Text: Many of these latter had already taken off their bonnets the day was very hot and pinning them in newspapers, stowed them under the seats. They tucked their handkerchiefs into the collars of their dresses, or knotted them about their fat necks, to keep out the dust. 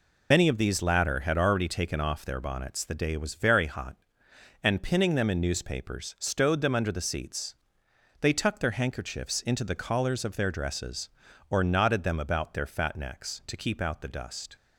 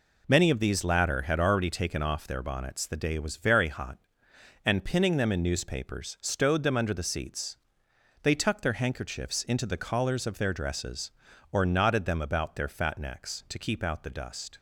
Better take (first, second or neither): second